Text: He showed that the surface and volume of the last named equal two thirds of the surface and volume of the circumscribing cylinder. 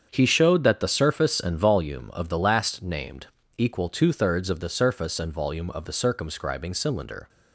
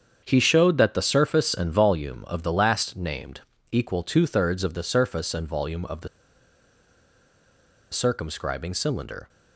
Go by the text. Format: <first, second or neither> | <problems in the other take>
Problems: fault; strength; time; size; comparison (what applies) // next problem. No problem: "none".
first | starts louder than the rest; strong; until 1.2 s; 7.5 dB; strong in the first // pauses between "named" and "equal"; slight; at 3.4 s; 0.30 s long; slight in the first // pauses between "the" and "circumscribing"; strong; at 6.0 s; 1.8 s long